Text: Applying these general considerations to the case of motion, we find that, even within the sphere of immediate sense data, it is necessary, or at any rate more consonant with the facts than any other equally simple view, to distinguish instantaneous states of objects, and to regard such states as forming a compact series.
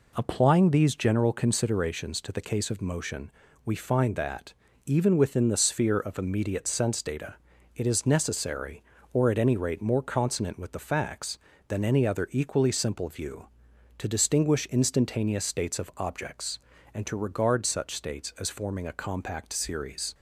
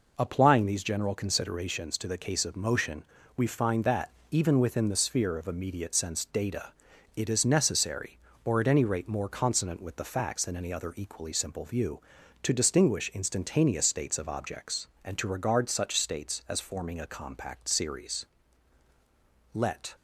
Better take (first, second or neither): first